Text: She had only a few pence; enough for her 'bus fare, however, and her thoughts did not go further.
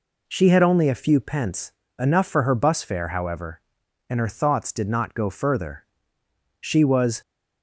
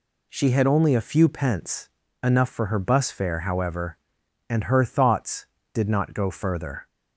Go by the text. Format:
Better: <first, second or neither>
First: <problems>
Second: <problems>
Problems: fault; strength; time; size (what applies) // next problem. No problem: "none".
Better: second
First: goes on to say "She was"; noticeable; from 6.5 s on; 0.62 s long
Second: none